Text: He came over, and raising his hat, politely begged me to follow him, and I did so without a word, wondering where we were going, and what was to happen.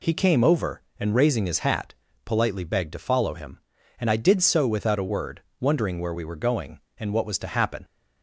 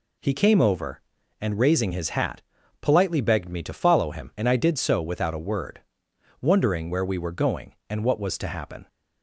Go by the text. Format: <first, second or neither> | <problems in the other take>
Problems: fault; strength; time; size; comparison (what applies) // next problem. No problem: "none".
second | skips "me"; at 2.9 s